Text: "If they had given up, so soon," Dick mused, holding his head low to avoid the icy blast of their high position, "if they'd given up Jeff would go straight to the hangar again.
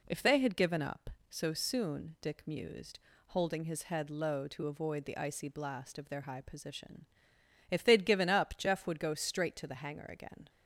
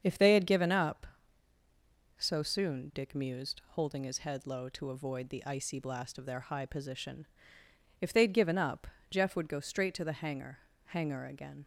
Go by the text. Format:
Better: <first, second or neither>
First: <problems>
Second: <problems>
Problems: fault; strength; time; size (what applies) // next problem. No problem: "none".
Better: first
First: none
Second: starts louder than the rest; strong; until 1.0 s; 7 dB // pauses between "up" and "Jeff"; slight; at 8.8 s; 0.22 s long // says "hangar" twice; at 10.8 s